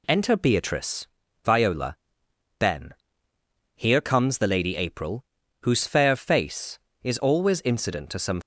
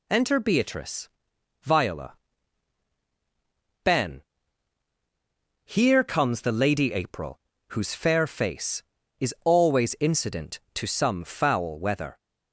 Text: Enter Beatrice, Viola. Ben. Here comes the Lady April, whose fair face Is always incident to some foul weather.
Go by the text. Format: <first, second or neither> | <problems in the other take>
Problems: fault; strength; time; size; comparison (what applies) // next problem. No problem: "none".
second | stops before "foul weather"; at 8.4 s